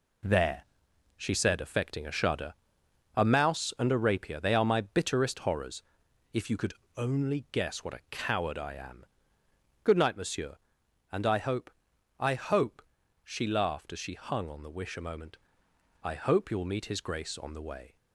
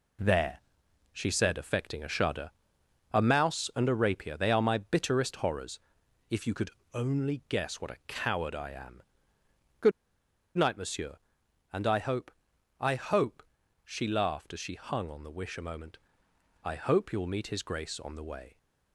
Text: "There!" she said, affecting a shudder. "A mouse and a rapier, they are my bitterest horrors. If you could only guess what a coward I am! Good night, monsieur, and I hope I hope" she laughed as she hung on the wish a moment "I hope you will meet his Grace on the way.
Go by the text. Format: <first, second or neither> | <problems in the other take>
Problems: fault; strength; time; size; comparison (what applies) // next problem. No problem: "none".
first | pauses between "could" and "only"; slight; at 6.6 s; 0.22 s long; slight in the first // pauses between "Good" and "night"; noticeable; at 9.9 s; 0.66 s long // pauses between "hope" and "I"; noticeable; at 12.3 s; 0.50 s long; noticeable in the first // pauses between "hope" and "she"; at 13.4 s; 0.42 s long; also in the first // pauses between "moment" and "I"; noticeable; at 15.9 s; 0.66 s long; noticeable in the first